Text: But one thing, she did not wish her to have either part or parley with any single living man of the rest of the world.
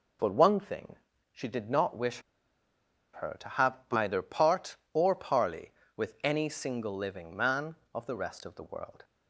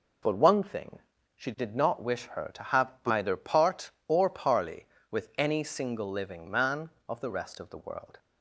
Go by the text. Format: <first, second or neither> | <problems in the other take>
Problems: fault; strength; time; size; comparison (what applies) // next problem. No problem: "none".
second | pauses between "wish" and "her"; noticeable; at 2.2 s; 0.92 s long // pauses between "have" and "either"; slight; at 3.7 s; 0.16 s long; slight in the second